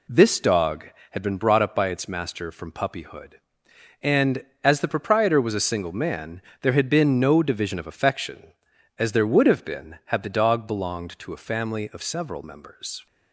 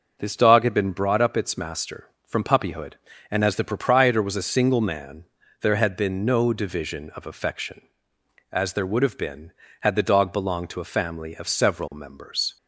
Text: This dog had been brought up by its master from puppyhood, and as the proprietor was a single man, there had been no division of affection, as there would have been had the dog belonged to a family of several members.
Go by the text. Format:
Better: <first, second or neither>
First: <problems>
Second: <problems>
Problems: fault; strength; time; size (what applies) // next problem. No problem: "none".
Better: first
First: none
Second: skips "by"; at 1.3 s